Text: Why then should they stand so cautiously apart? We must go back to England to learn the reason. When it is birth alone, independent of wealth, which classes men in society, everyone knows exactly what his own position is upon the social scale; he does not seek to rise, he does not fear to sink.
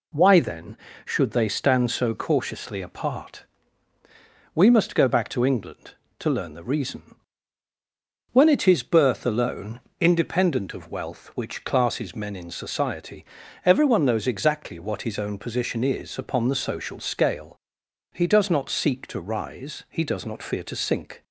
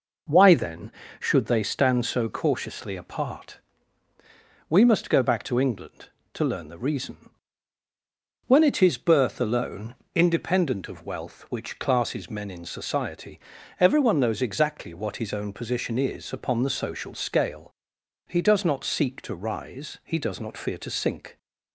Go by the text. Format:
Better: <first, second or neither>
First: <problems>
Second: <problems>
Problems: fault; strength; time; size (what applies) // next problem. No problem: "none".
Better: first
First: none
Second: starts louder than the rest; noticeable; until 1.6 s; 5 dB